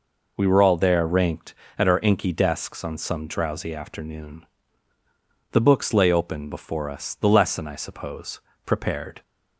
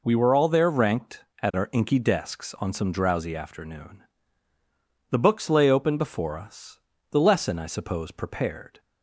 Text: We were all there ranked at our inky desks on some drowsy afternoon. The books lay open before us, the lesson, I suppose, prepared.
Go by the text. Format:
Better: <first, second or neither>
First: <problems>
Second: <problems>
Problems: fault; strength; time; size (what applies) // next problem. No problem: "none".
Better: neither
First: none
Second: none